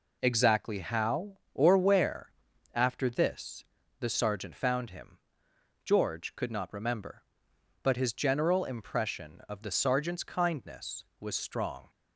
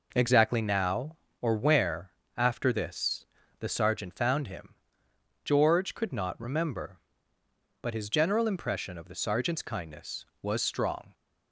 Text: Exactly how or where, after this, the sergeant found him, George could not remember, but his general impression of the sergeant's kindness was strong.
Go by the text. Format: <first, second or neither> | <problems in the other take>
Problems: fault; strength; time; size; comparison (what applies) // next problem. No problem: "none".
first | says "now" for "how"; at 0.6 s